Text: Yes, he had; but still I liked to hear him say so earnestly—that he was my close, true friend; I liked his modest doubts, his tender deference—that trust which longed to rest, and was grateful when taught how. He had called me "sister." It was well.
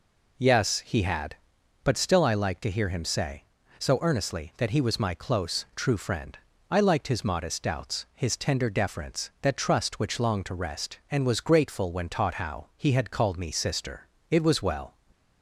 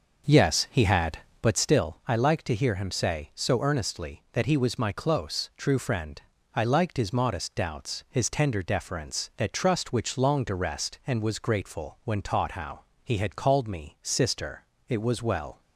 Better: first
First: none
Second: starts louder than the rest; noticeable; until 1.7 s; 6 dB

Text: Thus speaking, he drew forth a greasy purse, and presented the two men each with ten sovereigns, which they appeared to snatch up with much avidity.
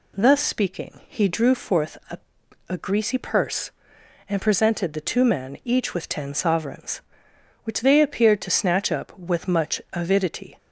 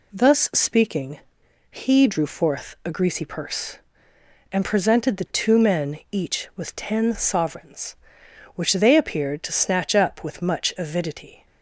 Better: second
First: says "a" twice; at 2.6 s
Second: none

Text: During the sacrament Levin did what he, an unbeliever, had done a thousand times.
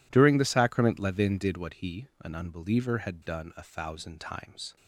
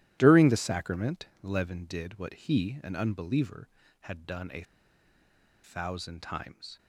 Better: first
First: none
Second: starts louder than the rest; strong; until 1.2 s; 13.5 dB // pauses between "sacrament" and "Levin"; slight; at 1.2 s; 0.16 s long // pauses between "a" and "thousand"; at 4.6 s; 1.0 s long

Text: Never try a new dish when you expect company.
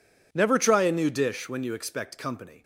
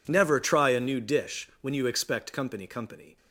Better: first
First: none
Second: says "company" twice; at 2.6 s

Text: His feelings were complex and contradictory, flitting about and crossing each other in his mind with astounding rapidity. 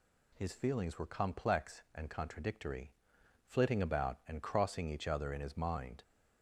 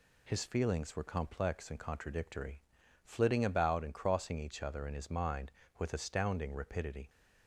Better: second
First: stops before "with astounding rapidity"; at 6.0 s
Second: none

